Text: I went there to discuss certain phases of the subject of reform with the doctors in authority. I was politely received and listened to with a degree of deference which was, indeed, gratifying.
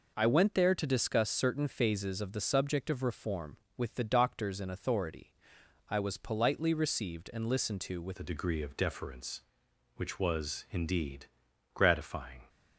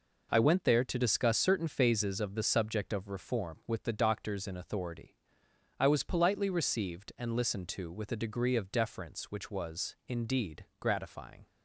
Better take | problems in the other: second | changes voice at "a"; from 8.1 s on; 4.3 s long

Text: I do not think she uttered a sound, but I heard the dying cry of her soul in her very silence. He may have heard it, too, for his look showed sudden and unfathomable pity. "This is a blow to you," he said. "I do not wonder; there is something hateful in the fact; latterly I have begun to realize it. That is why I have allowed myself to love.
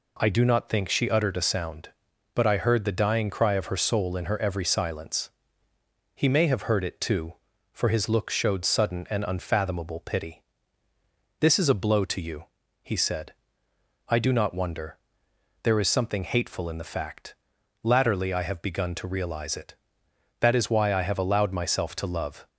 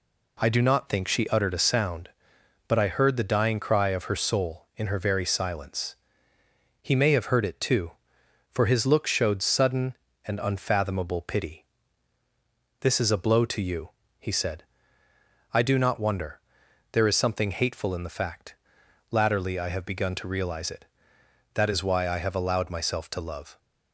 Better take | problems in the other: second | says "every" for "very"; at 4.4 s

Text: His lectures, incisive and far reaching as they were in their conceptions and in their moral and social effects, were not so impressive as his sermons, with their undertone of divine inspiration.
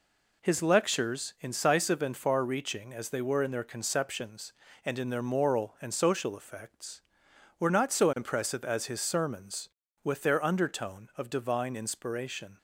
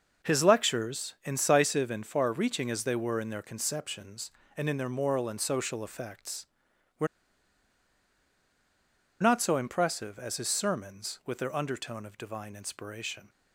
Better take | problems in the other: first | pauses between "were" and "not"; strong; at 7.0 s; 2.1 s long

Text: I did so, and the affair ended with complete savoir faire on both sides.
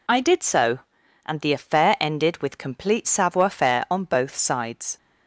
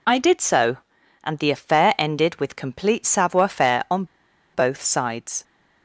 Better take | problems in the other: first | pauses between "on" and "both"; noticeable; at 4.0 s; 0.49 s long

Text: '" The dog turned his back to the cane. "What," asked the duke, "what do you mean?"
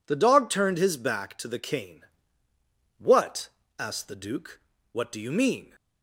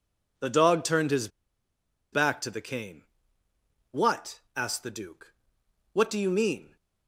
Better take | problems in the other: first | pauses between "his" and "back"; noticeable; at 1.2 s; 0.84 s long

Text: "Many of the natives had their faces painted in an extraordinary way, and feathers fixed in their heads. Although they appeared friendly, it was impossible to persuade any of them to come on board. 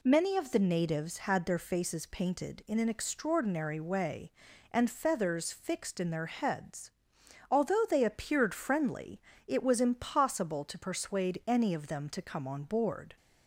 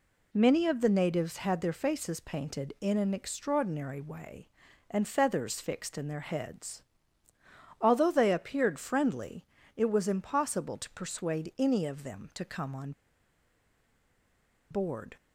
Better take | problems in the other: first | pauses between "on" and "board"; strong; at 12.9 s; 1.7 s long

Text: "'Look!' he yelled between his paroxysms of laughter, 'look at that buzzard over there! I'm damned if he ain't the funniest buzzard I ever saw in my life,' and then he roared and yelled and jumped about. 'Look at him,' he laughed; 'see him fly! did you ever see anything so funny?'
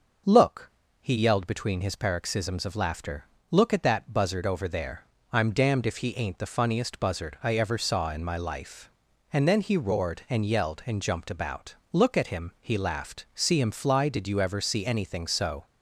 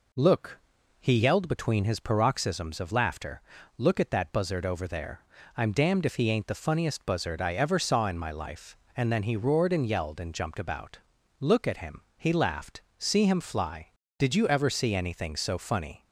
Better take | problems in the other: second | stops before "funny"; at 15.6 s

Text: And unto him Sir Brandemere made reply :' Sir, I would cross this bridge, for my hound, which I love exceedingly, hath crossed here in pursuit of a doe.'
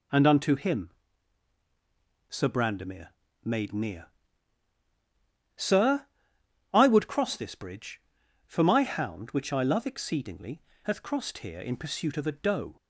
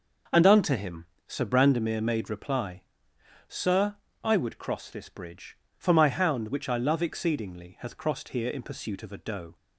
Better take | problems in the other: second | pauses between "him" and "Sir"; strong; at 0.8 s; 1.4 s long; slight in the second // pauses between "Brandemere" and "made"; slight; at 3.0 s; 0.34 s long // says "near" for "reply"; at 3.7 s

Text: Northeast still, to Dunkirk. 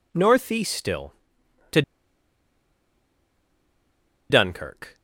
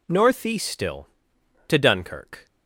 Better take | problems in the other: second | pauses between "to" and "Dunkirk"; strong; at 1.8 s; 2.4 s long

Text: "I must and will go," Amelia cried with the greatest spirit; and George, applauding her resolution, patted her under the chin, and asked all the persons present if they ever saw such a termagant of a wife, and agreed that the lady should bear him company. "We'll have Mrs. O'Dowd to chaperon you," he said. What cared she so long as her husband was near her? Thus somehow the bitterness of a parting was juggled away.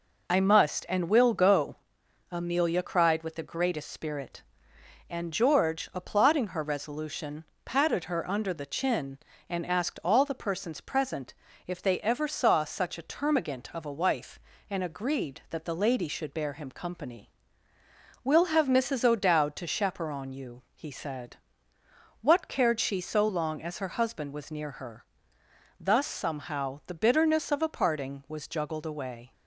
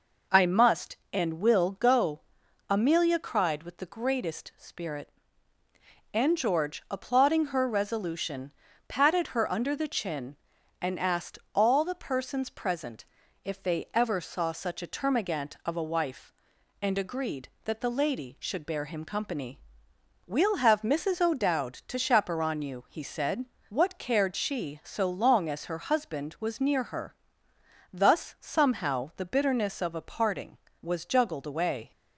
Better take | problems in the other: neither | pauses between "present" and "if"; the same in both

